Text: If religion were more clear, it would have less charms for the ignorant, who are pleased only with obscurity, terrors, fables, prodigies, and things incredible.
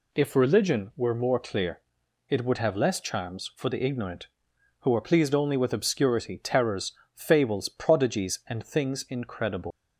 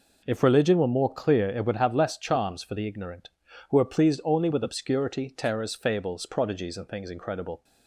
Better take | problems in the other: second | leaves "incredible" unfinished; at 9.7 s; 120 ms

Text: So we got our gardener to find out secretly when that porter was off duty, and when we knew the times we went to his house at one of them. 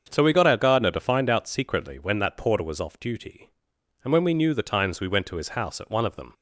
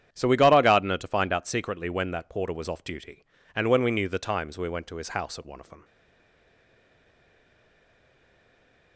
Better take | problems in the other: first | starts louder than the rest; strong; until 1.1 s; 9.5 dB; also in the first // stays silent after the last word; strong; from 5.8 s on; 3.1 s long

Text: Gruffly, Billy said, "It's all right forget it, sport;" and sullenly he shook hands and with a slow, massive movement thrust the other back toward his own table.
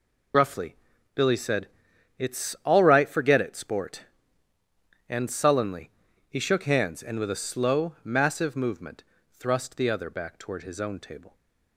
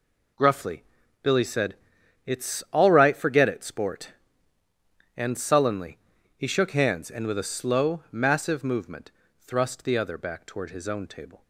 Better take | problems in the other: second | loses the start of "Gruffly"; at 0.3 s; 60 ms // pauses between "sullenly" and "he"; at 5.9 s; 0.40 s long; also in the second // pauses between "movement" and "thrust"; slight; at 9.0 s; 0.30 s long; slight in the second

